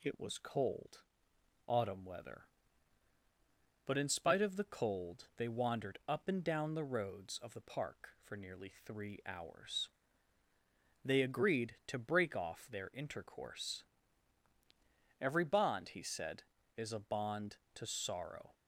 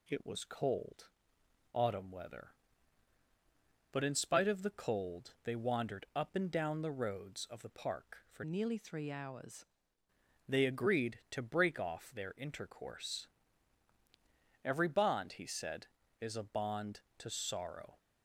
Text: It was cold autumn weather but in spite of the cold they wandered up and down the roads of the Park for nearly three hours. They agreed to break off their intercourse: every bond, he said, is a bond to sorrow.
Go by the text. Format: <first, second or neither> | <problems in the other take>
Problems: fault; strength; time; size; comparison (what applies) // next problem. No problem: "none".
first | pauses between "cold" and "autumn"; noticeable; at 1.0 s; 0.68 s long; noticeable in the first // changes voice from "nearly" to "hours"; from 8.4 to 9.6 s; 1.2 s long